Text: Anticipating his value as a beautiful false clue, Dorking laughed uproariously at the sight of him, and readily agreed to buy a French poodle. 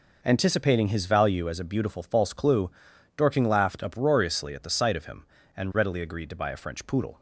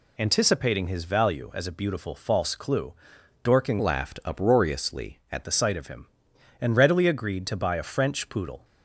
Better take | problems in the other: first | changes voice from "laughed" to "at"; from 3.7 to 5.4 s; 1.7 s long

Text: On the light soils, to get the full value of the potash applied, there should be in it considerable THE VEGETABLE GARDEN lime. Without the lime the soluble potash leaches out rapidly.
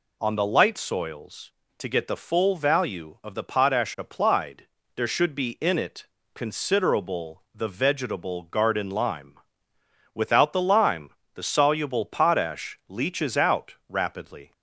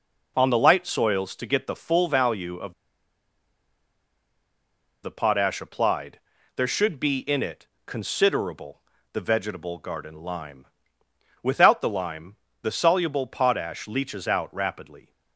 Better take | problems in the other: first | pauses between "of" and "the"; strong; at 2.7 s; 2.3 s long // pauses between "it" and "considerable"; slight; at 7.6 s; 0.18 s long; slight in the first // pauses between "considerable" and "THE"; slight; at 8.8 s; 0.32 s long // pauses between "lime" and "the"; slight; at 12.3 s; 0.26 s long; slight in the first

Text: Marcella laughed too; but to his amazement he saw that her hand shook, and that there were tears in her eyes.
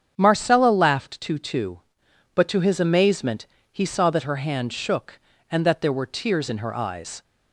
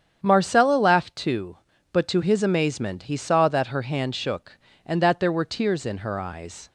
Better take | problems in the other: second | starts louder than the rest; strong; until 1.1 s; 7.5 dB; strong in the second // says "too" twice; at 1.3 s // pauses between "amazement" and "he"; slight; at 3.4 s; 0.24 s long

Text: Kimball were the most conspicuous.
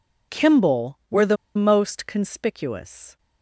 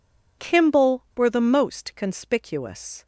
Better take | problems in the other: second | pauses between "the" and "most"; slight; at 1.3 s; 0.21 s long

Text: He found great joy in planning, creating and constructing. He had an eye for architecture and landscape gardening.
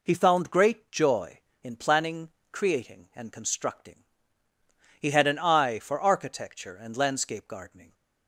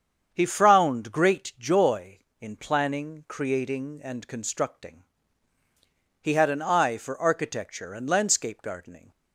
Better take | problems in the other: first | starts louder than the rest; strong; until 1.3 s; 7.5 dB // says "frowned" for "found"; at 0.4 s

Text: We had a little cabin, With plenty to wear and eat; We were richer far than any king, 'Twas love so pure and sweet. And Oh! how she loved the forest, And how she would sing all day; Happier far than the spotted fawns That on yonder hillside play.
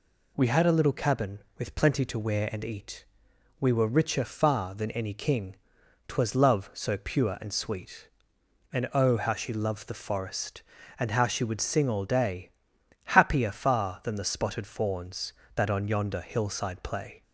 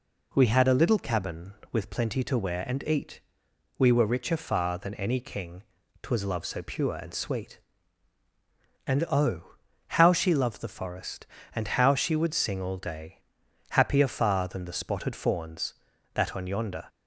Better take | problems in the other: first | stops before "hillside play"; at 16.8 s

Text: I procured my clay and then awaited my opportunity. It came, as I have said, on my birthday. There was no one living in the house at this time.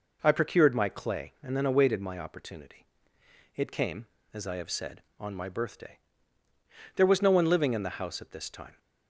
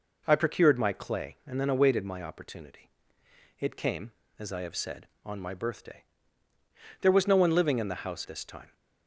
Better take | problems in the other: first | skips "at"; at 8.2 s

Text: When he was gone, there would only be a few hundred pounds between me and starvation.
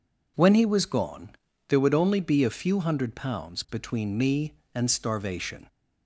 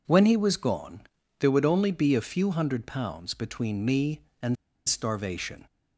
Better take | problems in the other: first | pauses between "and" and "starvation"; slight; at 4.5 s; 0.31 s long

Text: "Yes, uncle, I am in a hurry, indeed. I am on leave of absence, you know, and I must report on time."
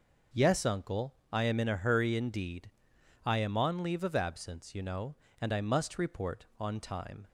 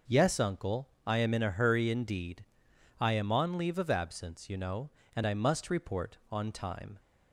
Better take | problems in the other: neither | none

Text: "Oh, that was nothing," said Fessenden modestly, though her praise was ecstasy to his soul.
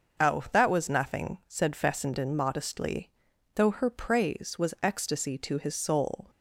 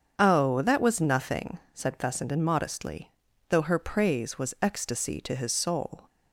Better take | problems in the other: neither | starts louder than the rest; the same in both

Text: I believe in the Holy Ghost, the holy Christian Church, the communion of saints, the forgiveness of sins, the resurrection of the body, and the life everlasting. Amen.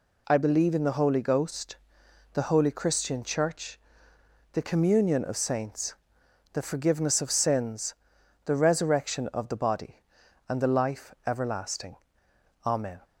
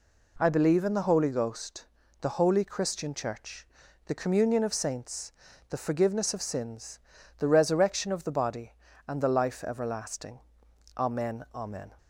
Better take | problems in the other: first | says "Amen" twice; at 11.5 s

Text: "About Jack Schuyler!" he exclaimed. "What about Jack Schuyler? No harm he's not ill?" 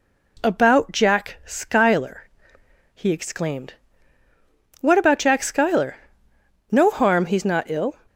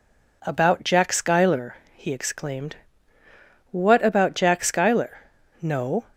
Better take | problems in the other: first | stops before "harm he's not ill"; at 6.1 s

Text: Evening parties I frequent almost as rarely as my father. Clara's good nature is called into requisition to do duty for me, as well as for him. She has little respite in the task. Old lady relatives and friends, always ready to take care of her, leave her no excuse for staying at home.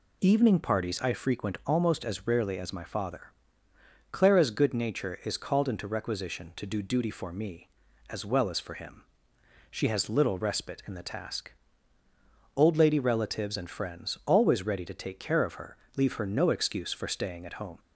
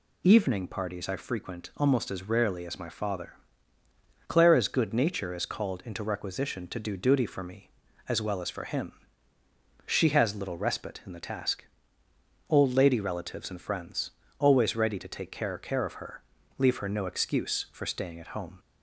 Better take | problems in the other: first | says "care" twice; at 15.5 s

